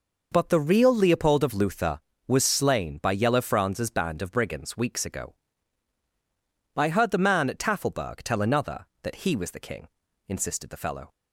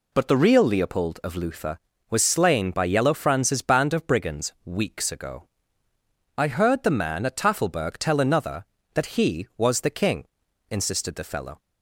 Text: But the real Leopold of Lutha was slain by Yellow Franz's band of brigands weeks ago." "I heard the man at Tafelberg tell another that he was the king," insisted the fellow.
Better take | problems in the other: neither | none

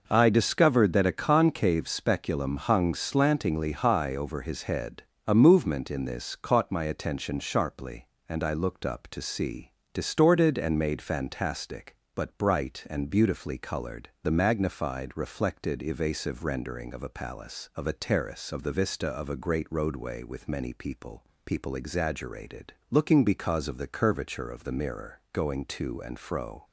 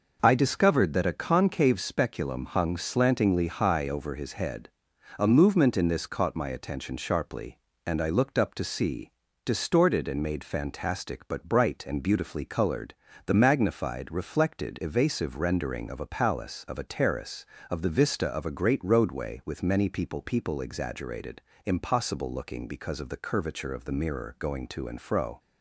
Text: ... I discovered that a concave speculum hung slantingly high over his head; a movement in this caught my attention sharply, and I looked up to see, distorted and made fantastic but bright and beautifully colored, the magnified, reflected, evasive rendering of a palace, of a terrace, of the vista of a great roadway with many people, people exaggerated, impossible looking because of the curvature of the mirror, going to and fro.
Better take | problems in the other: second | skips "impossible"; at 22.8 s

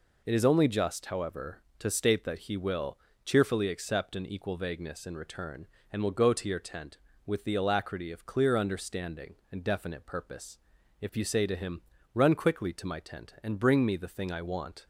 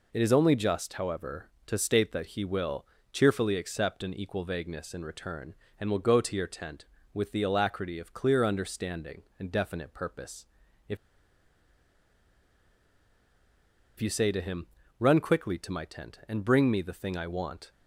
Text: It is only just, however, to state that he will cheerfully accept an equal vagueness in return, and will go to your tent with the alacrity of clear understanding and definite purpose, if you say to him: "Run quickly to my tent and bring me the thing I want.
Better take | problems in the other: first | pauses between "will" and "cheerfully"; slight; at 2.8 s; 0.26 s long; slight in the first // pauses between "if" and "you"; strong; at 10.9 s; 3.0 s long

